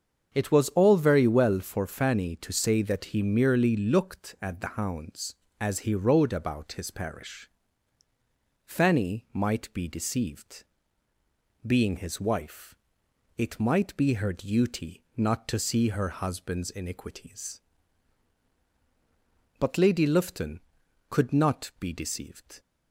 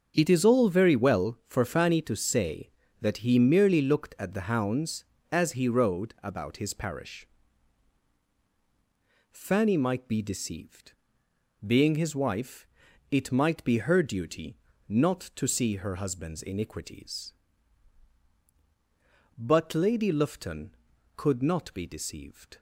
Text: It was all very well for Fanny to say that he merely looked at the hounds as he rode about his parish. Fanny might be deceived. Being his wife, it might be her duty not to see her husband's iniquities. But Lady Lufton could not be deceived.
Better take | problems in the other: first | starts louder than the rest; until 1.1 s; 7 dB; also in the first // says "is" for "was"; at 0.2 s // pauses between "duty" and "not"; slight; at 14.5 s; 0.32 s long

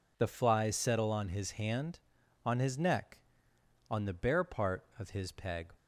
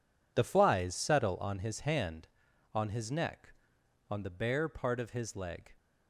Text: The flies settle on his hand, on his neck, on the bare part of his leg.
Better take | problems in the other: second | says "peg" for "leg"; at 5.3 s

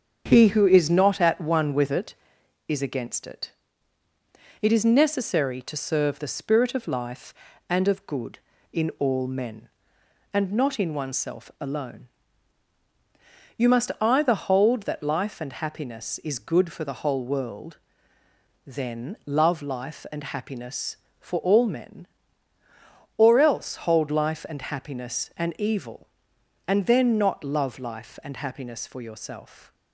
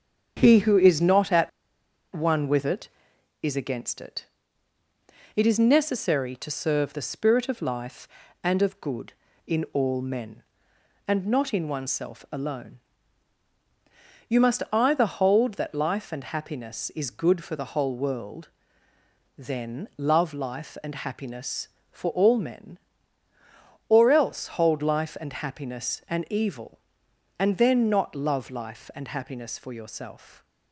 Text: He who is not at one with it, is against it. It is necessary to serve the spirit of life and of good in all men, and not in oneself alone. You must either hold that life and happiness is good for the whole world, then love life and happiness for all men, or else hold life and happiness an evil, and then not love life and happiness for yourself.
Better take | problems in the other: first | starts louder than the rest; strong; until 1.4 s; 7.5 dB; strong in the first // pauses between "at" and "one"; noticeable; at 1.4 s; 0.64 s long

